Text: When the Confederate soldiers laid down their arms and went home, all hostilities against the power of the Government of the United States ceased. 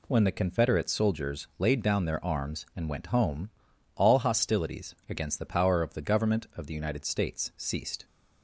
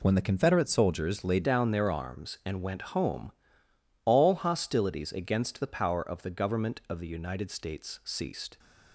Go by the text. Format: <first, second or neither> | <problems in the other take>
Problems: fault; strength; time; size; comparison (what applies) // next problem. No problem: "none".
first | changes voice at "down"; from 1.4 s on; 7.1 s long